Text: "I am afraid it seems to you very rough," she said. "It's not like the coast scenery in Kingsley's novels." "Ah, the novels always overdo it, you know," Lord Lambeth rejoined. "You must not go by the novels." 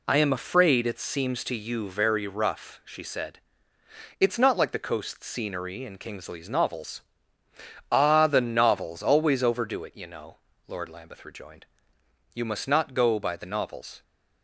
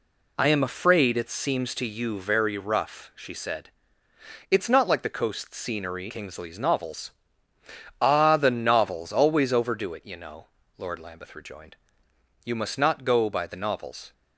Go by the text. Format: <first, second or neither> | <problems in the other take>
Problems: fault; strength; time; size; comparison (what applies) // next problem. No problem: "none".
first | skips "in"; at 6.0 s